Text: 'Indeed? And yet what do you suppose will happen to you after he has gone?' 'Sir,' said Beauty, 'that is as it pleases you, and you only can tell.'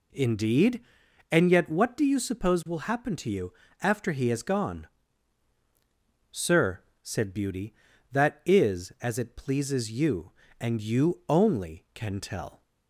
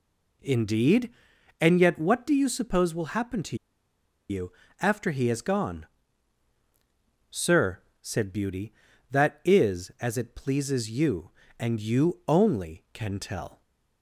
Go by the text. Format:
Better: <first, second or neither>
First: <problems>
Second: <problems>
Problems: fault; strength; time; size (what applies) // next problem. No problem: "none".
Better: first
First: pauses between "you" and "after"; slight; at 3.5 s; 0.30 s long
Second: pauses between "to" and "you"; noticeable; at 3.5 s; 0.73 s long // pauses between "you" and "after"; slight; at 4.5 s; 0.30 s long